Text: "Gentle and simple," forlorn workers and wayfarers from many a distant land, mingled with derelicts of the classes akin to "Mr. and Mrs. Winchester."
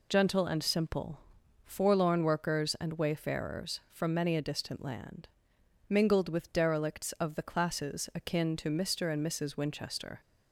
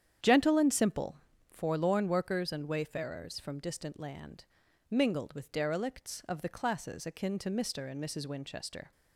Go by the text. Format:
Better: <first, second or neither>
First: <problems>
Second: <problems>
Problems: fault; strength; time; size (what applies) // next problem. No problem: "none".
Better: first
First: none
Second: starts louder than the rest; strong; until 1.5 s; 9 dB // skips "many a"; at 3.5 s